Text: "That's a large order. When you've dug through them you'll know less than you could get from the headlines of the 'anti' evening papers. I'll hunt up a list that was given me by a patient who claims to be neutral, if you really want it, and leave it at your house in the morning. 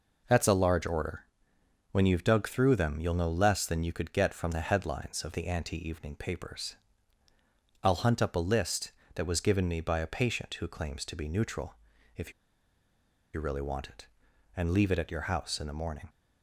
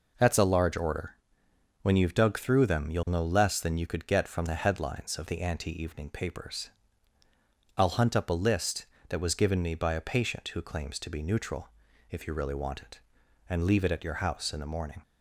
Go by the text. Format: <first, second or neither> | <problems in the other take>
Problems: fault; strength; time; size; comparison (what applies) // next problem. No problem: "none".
second | pauses between "if" and "you"; at 12.3 s; 1.0 s long